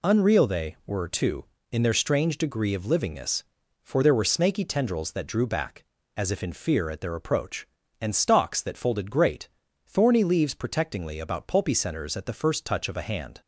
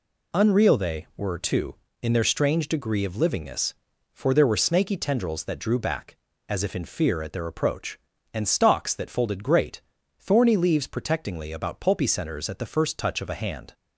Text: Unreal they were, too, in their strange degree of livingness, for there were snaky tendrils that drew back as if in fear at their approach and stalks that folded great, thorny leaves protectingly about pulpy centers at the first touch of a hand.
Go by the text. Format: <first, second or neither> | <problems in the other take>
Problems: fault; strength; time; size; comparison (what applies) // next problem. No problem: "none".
neither | none